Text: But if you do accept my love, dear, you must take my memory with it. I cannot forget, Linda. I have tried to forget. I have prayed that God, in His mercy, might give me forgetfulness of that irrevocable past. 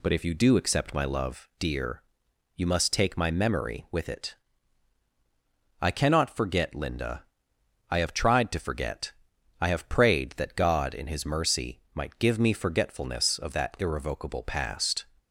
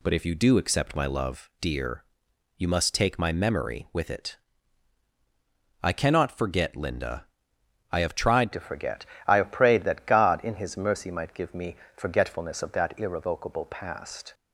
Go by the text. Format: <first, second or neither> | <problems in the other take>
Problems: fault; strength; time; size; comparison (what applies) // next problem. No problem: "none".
first | changes voice at "to"; from 8.5 s on; 5.8 s long // pauses between "me" and "forgetfulness"; slight; at 11.7 s; 0.20 s long